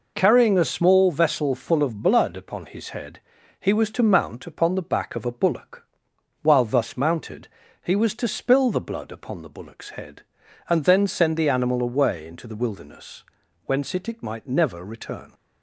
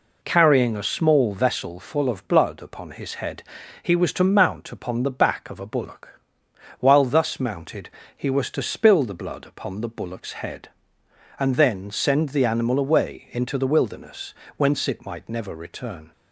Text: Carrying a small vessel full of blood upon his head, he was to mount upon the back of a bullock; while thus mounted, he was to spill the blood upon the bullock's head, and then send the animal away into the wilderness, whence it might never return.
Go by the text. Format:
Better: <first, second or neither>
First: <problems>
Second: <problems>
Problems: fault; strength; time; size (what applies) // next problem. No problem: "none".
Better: second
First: says "it" twice; at 14.0 s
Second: none